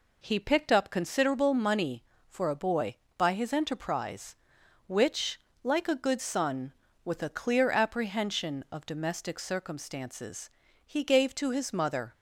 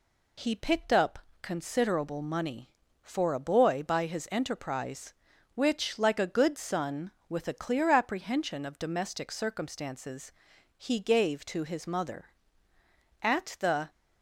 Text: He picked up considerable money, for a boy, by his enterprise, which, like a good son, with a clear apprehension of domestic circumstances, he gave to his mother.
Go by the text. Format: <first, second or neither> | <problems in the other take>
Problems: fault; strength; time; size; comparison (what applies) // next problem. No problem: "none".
first | pauses between "up" and "considerable"; slight; at 1.1 s; 0.24 s long // goes on to say "At the"; noticeable; from 13.1 s on; 0.70 s long